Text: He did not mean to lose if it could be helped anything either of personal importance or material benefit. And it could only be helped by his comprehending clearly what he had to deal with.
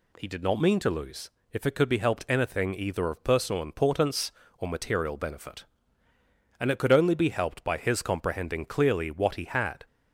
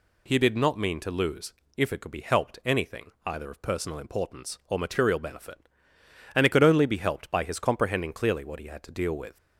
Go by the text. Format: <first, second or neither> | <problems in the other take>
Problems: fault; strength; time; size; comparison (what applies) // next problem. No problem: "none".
second | pauses between "lose" and "if"; slight; at 1.2 s; 0.22 s long; slight in the second // stops before "to deal with"; at 9.8 s